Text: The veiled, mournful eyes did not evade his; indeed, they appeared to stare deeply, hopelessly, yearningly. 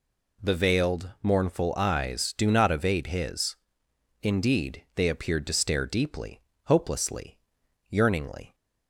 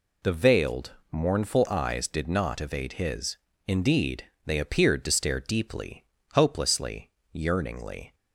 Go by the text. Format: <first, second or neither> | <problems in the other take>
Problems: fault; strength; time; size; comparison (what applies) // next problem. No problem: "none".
second | says "do" for "did"; at 2.3 s